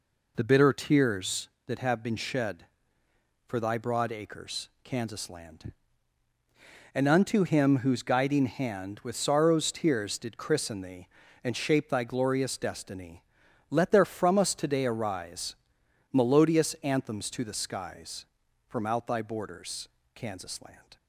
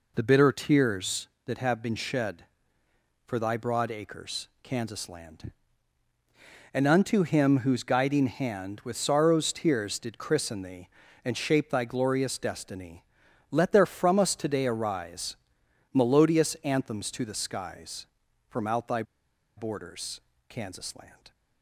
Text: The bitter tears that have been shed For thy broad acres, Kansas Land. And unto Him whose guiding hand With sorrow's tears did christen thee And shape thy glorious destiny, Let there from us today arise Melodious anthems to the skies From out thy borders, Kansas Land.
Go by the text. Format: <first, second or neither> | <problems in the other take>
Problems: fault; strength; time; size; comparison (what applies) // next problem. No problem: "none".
first | pauses between "arise" and "Melodious"; noticeable; at 15.3 s; 0.58 s long; noticeable in the first // pauses between "thy" and "borders"; noticeable; at 19.0 s; 0.53 s long